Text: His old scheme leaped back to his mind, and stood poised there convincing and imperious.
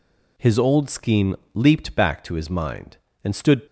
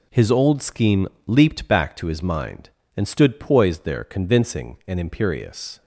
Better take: second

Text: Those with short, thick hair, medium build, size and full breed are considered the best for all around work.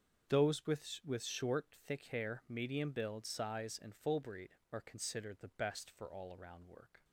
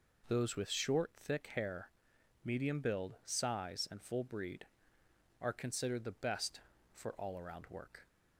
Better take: second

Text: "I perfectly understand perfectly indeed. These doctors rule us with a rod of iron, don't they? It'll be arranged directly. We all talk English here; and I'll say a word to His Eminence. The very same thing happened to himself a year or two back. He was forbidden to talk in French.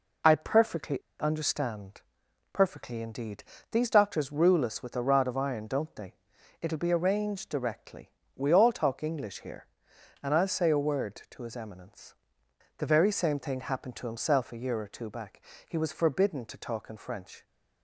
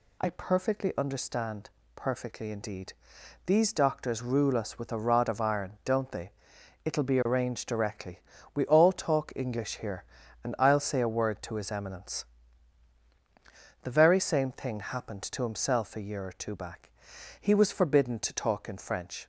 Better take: second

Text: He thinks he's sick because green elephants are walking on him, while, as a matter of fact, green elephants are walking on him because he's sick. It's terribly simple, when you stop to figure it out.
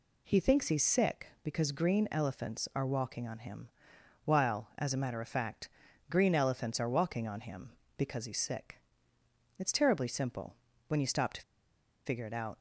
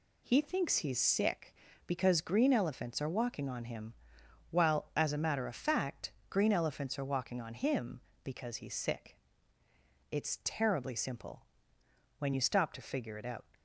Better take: second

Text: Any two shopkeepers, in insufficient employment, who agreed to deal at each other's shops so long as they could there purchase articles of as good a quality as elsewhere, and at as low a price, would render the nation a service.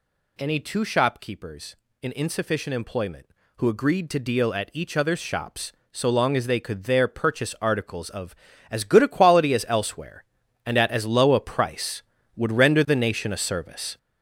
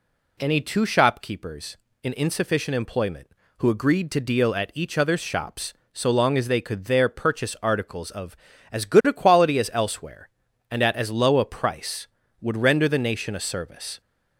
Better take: second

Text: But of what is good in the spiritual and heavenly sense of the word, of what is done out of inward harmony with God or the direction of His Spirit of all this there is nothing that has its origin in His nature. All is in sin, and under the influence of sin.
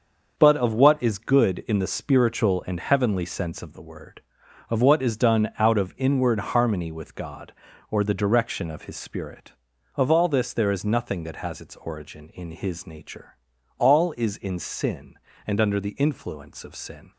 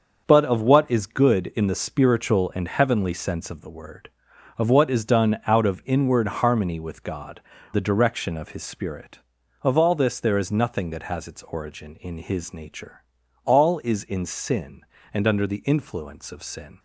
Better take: first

